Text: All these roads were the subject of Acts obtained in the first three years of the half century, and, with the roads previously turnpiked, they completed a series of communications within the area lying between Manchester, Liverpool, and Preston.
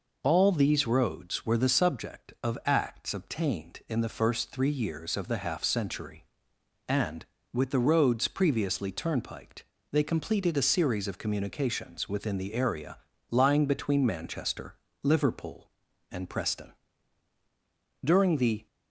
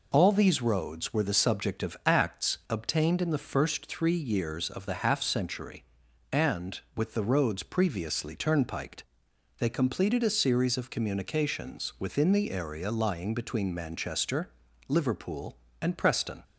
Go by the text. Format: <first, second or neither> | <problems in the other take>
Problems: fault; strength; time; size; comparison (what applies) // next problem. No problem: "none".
second | pauses between "area" and "lying"; slight; at 12.9 s; 0.32 s long // goes on to say "During the"; noticeable; from 18.0 s on; 0.62 s long